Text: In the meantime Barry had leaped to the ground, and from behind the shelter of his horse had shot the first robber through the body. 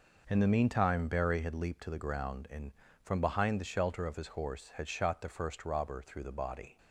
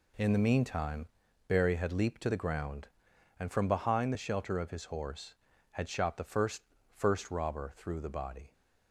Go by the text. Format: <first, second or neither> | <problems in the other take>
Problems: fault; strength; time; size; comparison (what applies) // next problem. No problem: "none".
first | pauses between "meantime" and "Barry"; at 1.0 s; 0.40 s long // says "first" twice; at 6.9 s